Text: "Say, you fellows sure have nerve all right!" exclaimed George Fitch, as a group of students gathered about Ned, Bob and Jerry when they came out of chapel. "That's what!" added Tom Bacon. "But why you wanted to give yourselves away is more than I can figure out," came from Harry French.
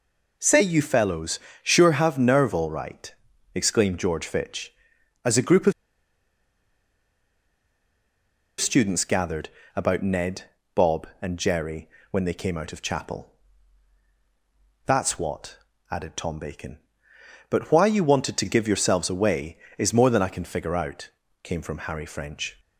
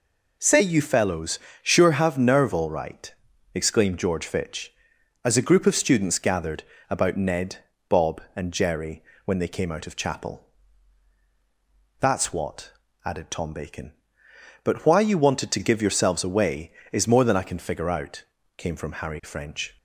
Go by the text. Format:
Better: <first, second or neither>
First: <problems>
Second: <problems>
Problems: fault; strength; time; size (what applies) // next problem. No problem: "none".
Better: second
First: pauses between "fellows" and "sure"; slight; at 1.3 s; 0.22 s long // pauses between "of" and "students"; strong; at 5.7 s; 2.8 s long // pauses between "gathered" and "about"; slight; at 9.4 s; 0.26 s long // pauses between "Jerry" and "when"; slight; at 11.8 s; 0.22 s long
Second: pauses between "fellows" and "sure"; slight; at 1.3 s; 0.22 s long // pauses between "gathered" and "about"; slight; at 6.6 s; 0.26 s long // pauses between "Jerry" and "when"; slight; at 9.0 s; 0.22 s long